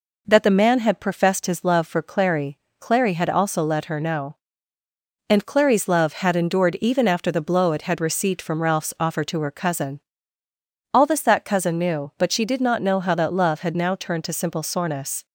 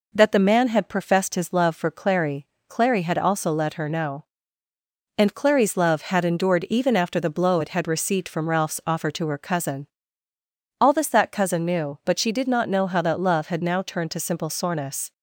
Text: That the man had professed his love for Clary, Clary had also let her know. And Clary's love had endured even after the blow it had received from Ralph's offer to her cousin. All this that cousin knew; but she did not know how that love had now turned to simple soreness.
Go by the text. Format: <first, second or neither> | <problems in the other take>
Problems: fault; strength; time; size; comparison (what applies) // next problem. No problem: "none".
neither | none